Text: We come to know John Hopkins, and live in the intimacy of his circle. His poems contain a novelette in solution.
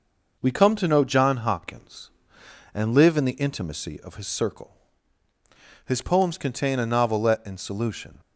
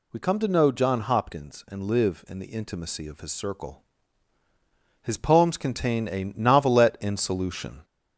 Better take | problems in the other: first | gets louder; slight; throughout; 2.5 dB

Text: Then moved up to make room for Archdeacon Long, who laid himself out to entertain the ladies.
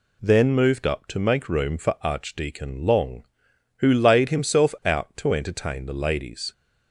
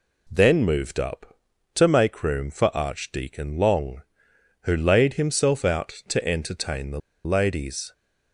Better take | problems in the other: first | pauses between "the" and "ladies"; slight; at 6.9 s; 0.24 s long

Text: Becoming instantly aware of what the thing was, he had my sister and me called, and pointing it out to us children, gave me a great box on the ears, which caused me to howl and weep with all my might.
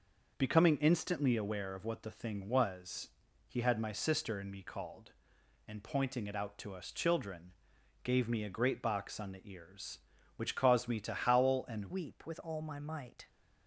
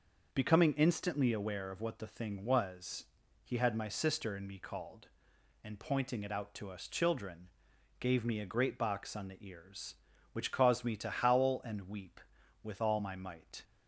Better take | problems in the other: second | changes voice at "weep"; from 11.9 s on; 1.3 s long

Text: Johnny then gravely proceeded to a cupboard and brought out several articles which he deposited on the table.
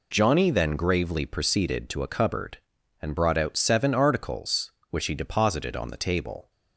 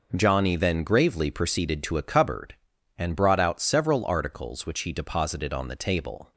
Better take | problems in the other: second | says "seven" for "several"; at 3.5 s

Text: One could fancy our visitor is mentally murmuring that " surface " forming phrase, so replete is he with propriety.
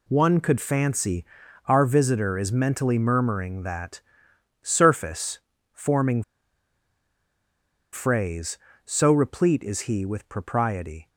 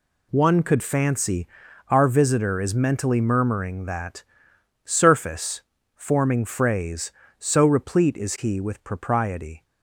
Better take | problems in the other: second | pauses between "fancy" and "our"; at 1.2 s; 0.40 s long; also in the second // pauses between "forming" and "phrase"; strong; at 6.2 s; 1.6 s long

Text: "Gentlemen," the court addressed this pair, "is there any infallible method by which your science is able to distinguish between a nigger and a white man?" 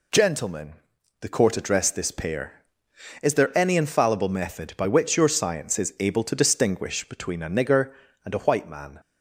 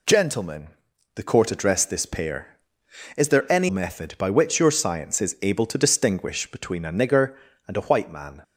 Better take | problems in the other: first | skips "infallible"; at 3.6 s

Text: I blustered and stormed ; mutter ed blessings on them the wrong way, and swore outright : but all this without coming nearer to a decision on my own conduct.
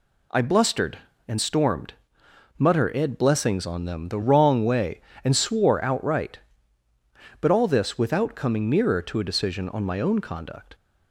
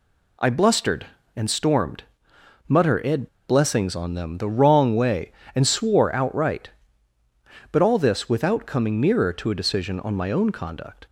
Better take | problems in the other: first | pauses between "ed" and "blessings"; slight; at 3.2 s; 0.22 s long

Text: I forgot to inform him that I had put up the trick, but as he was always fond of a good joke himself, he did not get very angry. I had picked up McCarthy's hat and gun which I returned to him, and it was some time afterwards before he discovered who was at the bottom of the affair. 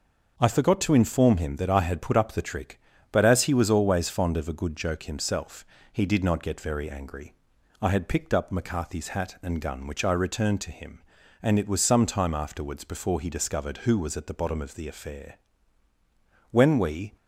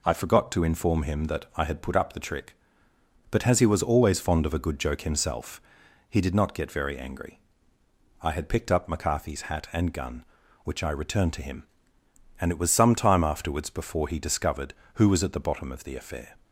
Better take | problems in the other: second | goes on to say "When we"; noticeable; from 16.4 s on; 0.66 s long

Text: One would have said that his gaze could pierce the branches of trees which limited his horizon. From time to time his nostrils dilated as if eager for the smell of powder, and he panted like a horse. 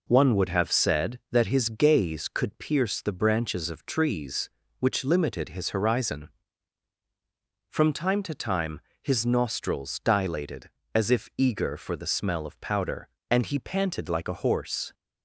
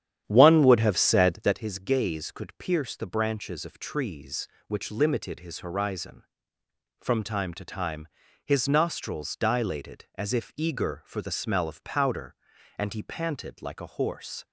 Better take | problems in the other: first | starts louder than the rest; strong; until 1.6 s; 10 dB // pauses between "time" and "his"; slight; at 8.0 s; 0.36 s long; slight in the first

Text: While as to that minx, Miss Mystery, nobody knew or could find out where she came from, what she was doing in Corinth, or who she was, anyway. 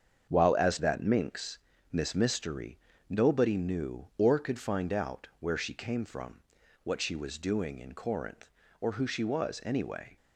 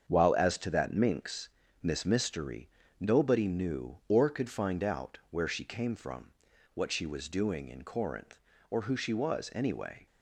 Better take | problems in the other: second | starts louder than the rest; strong; until 1.3 s; 7.5 dB; strong in the second // skips "to"; at 0.7 s

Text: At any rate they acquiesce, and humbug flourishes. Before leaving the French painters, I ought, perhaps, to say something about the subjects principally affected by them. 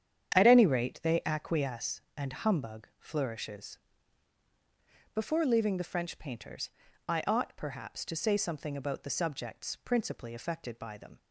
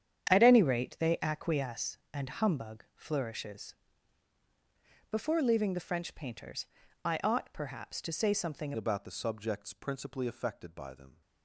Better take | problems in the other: first | starts louder than the rest; strong; until 1.3 s; 8.5 dB; strong in the first // changes voice at "about"; from 8.7 s on; 2.5 s long

